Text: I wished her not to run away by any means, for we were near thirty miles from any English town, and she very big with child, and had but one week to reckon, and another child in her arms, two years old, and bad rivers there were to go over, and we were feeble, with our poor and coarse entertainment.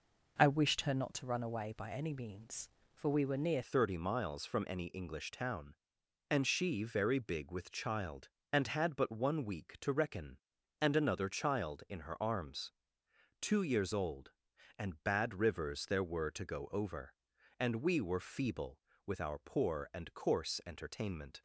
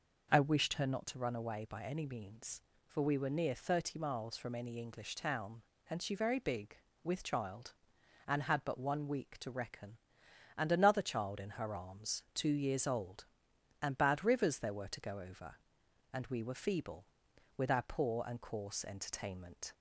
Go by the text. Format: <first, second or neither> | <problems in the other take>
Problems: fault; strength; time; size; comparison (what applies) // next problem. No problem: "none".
second | changes voice at "thirty"; from 3.6 s on; 17.8 s long